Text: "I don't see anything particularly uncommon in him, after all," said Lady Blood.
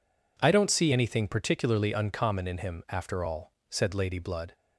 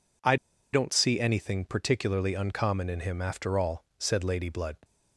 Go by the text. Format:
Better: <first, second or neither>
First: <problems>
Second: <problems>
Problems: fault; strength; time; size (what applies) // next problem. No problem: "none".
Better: first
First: none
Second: pauses between "I" and "don't"; at 0.3 s; 0.37 s long